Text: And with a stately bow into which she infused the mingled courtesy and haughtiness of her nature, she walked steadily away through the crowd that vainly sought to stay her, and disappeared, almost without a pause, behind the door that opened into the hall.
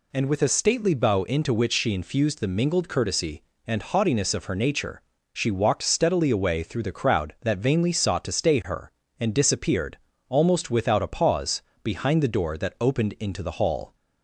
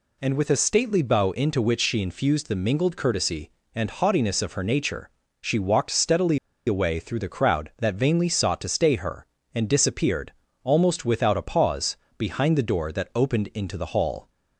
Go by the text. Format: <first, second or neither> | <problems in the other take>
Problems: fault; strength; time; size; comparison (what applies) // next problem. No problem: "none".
first | pauses between "steadily" and "away"; slight; at 6.3 s; 0.28 s long